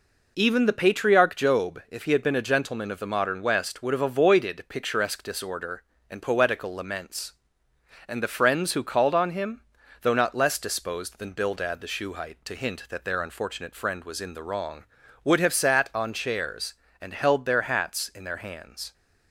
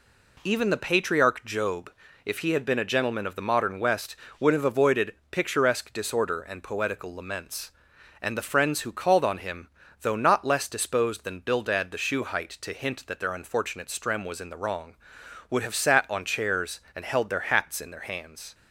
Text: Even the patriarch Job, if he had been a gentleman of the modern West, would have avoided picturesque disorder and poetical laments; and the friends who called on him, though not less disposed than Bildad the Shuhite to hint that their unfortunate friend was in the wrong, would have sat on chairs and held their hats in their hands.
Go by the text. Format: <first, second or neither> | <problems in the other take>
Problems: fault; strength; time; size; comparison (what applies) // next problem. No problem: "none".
first | pauses between "avoided" and "picturesque"; slight; at 5.1 s; 0.18 s long // says "strem" for "friend"; at 13.8 s